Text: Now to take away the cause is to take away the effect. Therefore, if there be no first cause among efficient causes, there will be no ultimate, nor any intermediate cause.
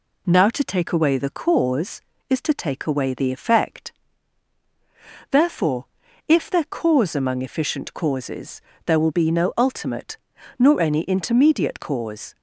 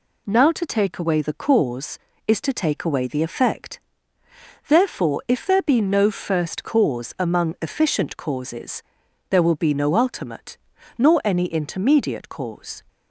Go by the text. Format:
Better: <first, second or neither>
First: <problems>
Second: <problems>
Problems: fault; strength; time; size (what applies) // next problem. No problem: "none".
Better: second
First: skips "be no first"; at 6.6 s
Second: none